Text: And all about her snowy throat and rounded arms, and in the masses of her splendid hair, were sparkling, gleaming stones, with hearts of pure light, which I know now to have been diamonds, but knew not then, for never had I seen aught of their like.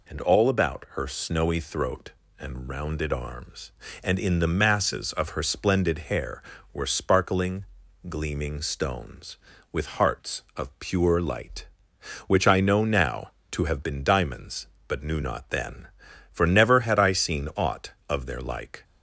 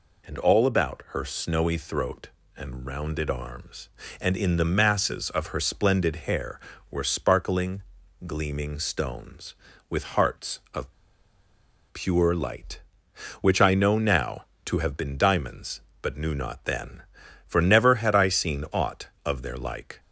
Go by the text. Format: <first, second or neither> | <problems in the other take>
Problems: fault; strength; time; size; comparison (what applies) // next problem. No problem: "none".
first | pauses between "of" and "pure"; at 10.9 s; 0.99 s long